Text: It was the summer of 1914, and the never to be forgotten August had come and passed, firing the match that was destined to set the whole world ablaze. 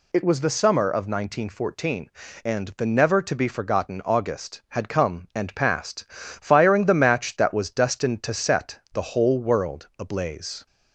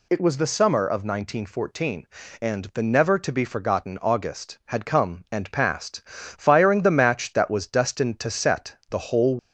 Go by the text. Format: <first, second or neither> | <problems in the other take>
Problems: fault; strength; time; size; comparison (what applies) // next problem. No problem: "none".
first | stops before "world ablaze"; at 9.3 s